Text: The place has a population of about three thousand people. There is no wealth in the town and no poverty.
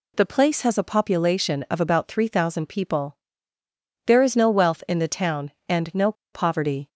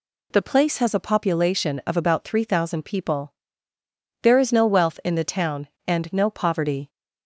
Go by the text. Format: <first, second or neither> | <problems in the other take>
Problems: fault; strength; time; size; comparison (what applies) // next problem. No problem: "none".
second | pauses between "no" and "poverty"; slight; at 6.1 s; 0.20 s long